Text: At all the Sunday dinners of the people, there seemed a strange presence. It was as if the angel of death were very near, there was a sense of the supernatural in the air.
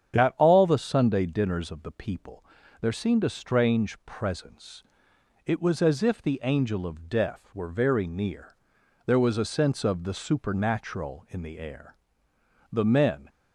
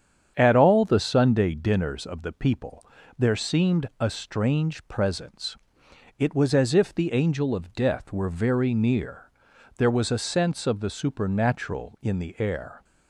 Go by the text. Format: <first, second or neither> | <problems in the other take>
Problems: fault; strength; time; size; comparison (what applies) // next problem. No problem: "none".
second | starts louder than the rest; strong; until 1.1 s; 8.5 dB; strong in the second // goes on to say "The men"; from 12.7 s on; 0.58 s long